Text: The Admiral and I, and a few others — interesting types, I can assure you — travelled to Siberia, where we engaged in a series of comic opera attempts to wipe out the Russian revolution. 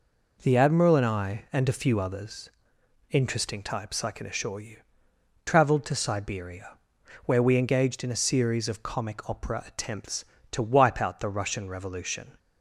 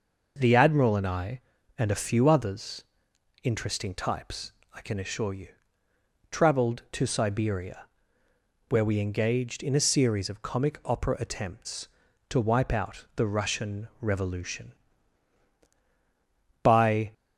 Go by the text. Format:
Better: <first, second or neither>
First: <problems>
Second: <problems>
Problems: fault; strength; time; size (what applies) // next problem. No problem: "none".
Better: first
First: none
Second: goes on to say "By"; from 16.6 s on; 0.52 s long